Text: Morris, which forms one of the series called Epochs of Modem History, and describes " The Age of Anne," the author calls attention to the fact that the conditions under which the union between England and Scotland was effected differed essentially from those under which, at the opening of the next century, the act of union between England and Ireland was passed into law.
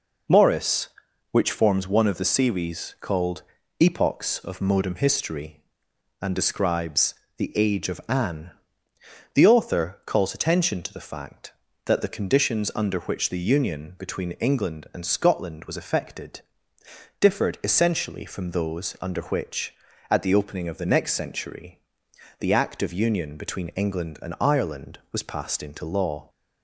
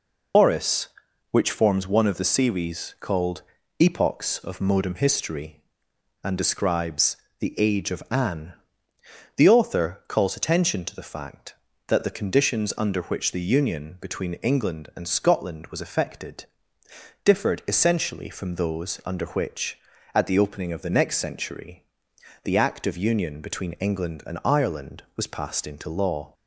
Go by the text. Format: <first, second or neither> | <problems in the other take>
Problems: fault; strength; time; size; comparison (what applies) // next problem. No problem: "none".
first | loses the start of "Morris"; at 0.3 s; 60 ms // pauses between "called" and "Epochs"; at 3.4 s; 0.38 s long; also in the first // pauses between "effected" and "differed"; noticeable; at 16.4 s; 0.78 s long; noticeable in the first